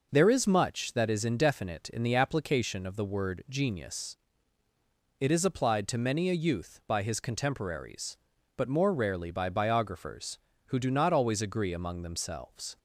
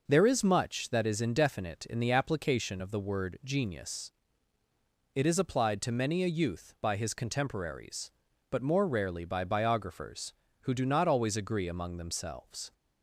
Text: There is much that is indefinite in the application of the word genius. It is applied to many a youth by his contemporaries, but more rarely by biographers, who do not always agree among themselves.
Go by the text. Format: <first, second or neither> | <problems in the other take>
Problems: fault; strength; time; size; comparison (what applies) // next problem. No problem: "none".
neither | none